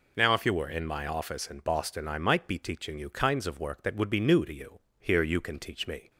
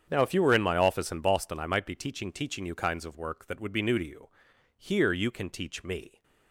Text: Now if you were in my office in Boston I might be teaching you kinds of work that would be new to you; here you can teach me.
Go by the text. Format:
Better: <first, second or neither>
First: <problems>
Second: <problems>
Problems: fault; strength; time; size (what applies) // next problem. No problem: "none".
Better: first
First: none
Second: starts louder than the rest; strong; until 1.1 s; 8 dB // says "teaching" twice; at 2.3 s